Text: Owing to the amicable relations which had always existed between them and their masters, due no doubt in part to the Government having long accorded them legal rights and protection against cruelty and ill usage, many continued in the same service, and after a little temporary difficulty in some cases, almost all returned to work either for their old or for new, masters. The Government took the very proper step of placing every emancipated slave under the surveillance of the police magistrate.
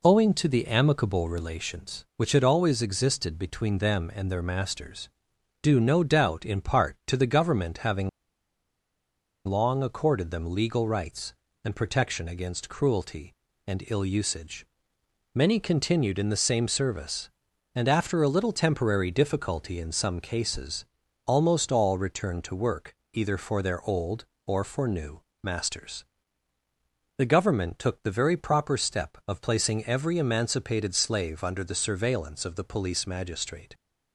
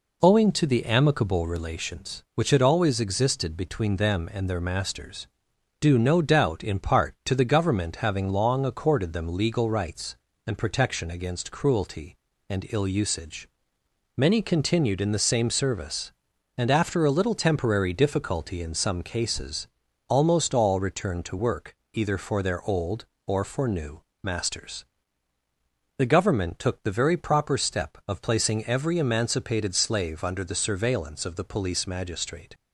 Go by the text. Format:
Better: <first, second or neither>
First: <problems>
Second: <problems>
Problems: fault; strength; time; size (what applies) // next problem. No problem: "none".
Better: second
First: pauses between "having" and "long"; strong; at 8.0 s; 1.3 s long // pauses between "work" and "either"; slight; at 22.9 s; 0.16 s long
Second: pauses between "work" and "either"; slight; at 21.7 s; 0.16 s long